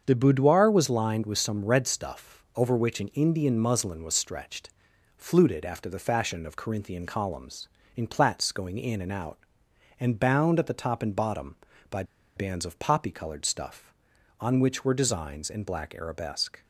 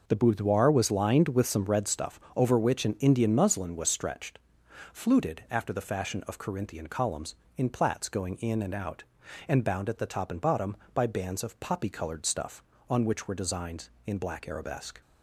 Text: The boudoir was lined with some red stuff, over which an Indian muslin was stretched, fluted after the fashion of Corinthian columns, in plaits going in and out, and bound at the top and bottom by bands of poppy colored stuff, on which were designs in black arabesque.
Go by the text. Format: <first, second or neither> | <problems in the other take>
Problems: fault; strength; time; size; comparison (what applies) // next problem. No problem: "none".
second | starts louder than the rest; until 1.0 s; 7 dB // pauses between "by" and "bands"; slight; at 12.0 s; 0.32 s long